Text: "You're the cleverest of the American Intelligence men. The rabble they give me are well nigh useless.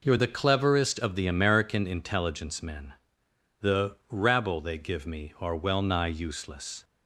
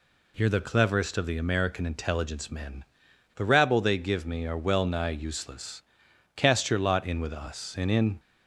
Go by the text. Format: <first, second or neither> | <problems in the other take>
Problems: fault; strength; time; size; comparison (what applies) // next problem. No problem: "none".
first | goes on to say "Cast your lot in with us and in"; strong; from 6.3 s on; 1.8 s long